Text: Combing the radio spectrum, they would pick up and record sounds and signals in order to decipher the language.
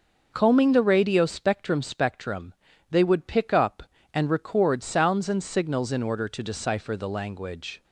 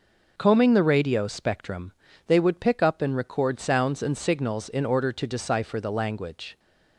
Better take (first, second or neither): second